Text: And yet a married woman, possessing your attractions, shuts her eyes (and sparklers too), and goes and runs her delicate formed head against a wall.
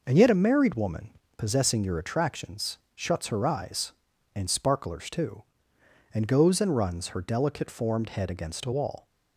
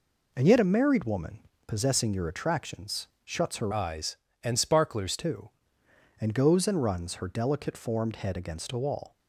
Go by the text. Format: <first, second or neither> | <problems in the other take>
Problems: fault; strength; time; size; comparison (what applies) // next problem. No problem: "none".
first | changes voice from "eyes" to "sparklers"; from 3.7 to 5.1 s; 1.4 s long